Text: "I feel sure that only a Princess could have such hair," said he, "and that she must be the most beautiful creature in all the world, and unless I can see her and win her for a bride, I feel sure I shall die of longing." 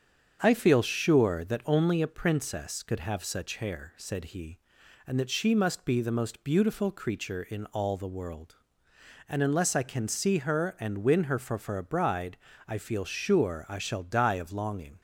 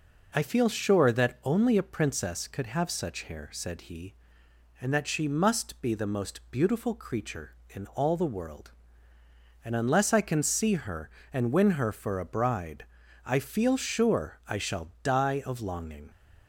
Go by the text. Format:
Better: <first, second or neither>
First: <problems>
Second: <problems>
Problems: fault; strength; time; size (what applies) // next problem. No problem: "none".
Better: second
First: starts louder than the rest; strong; until 1.4 s; 7 dB // says "for" twice; at 11.5 s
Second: none